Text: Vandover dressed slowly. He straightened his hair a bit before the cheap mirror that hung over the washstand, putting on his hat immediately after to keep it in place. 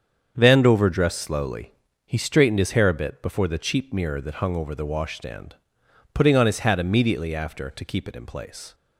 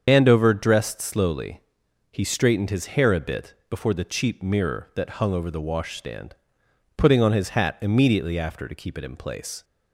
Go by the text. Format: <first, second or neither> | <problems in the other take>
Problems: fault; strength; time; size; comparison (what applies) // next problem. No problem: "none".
first | loses the start of "Vandover"; at 0.0 s; 110 ms // starts louder than the rest; strong; until 1.0 s; 7 dB; strong in the first // pauses between "bit" and "before"; slight; at 3.5 s; 0.16 s long